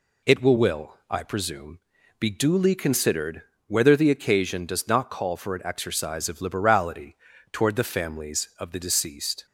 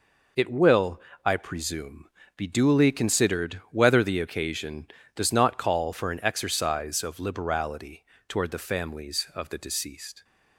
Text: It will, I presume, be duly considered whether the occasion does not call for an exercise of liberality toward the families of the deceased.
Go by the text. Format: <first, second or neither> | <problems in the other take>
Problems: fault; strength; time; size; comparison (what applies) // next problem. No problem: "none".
second | says "will" twice; at 0.5 s // pauses between "considered" and "whether"; slight; at 3.4 s; 0.26 s long // pauses between "liberality" and "toward"; slight; at 7.1 s; 0.36 s long; slight in the second